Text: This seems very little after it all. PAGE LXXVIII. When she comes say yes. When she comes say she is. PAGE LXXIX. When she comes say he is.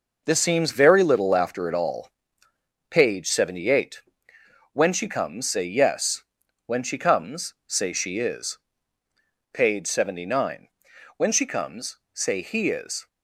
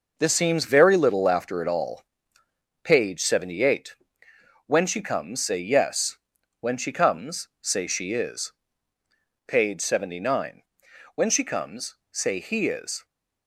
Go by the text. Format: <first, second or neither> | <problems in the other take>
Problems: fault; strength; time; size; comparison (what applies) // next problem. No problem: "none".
neither | none